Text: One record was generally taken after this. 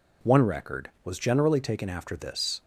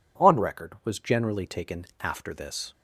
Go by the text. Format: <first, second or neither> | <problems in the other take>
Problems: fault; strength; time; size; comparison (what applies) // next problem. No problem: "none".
first | says "On" for "One"; at 0.1 s // pauses between "taken" and "after"; slight; at 1.8 s; 0.16 s long